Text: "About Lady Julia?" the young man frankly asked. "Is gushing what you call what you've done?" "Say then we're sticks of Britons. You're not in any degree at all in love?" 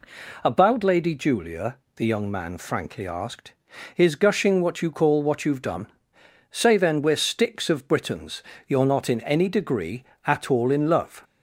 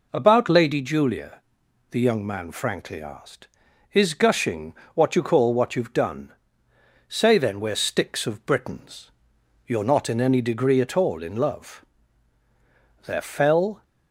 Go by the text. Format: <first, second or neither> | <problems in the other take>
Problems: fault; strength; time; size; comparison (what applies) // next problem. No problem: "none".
first | pauses between "gushing" and "what"; slight; at 4.7 s; 0.22 s long // goes on to say "There fell"; noticeable; from 13.0 s on; 0.78 s long